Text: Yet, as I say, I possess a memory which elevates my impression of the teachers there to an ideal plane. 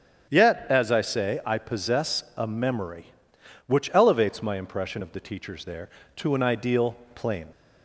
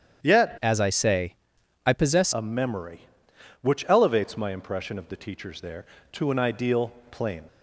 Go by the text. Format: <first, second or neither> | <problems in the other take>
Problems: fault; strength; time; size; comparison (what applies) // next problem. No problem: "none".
first | starts louder than the rest; strong; until 1.2 s; 9 dB; strong in the first // changes voice from "as" to "possess"; from 0.6 to 2.3 s; 1.7 s long // pauses between "ideal" and "plane"; slight; at 6.9 s; 0.18 s long; slight in the first